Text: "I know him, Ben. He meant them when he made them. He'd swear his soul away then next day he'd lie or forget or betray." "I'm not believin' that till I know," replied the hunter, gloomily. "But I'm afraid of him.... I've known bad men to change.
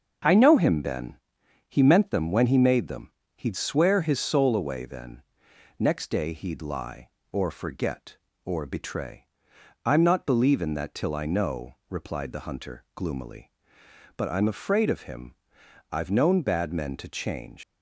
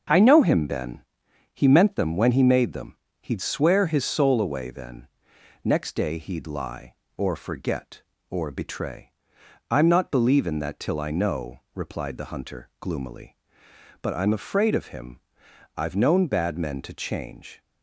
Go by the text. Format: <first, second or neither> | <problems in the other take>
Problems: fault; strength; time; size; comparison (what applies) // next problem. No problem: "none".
second | starts louder than the rest; noticeable; until 1.7 s; 6 dB; noticeable in the second // pauses between "then" and "next"; noticeable; at 5.2 s; 0.56 s long; noticeable in the second // leaves "change" unfinished; at 17.6 s; 120 ms